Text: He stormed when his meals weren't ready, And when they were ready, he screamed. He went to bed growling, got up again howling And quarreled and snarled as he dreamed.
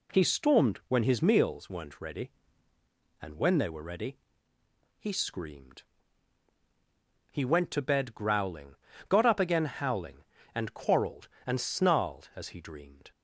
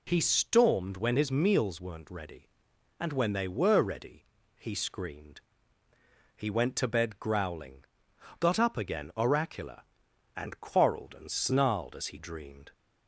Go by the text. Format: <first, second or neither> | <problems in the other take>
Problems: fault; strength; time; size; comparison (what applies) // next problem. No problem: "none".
first | says "oracular" for "howling"; at 9.1 s